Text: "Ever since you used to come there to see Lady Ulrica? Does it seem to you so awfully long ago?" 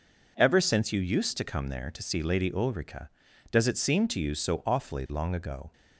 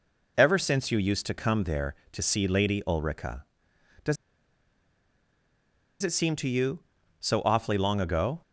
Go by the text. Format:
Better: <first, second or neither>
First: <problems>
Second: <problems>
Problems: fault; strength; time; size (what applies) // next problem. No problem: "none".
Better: first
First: none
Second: pauses between "Does" and "it"; strong; at 4.1 s; 1.8 s long